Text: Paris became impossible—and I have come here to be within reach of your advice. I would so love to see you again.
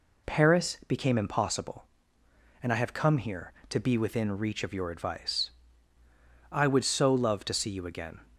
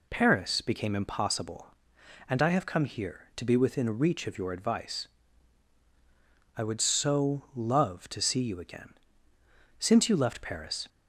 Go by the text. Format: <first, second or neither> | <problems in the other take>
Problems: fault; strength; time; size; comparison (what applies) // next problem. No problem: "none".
first | goes on to say "Since you left Paris"; noticeable; from 9.7 s on; 1.1 s long